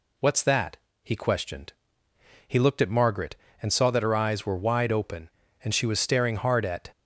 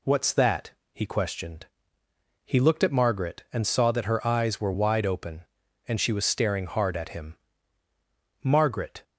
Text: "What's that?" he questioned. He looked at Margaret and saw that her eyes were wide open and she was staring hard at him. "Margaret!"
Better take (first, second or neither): second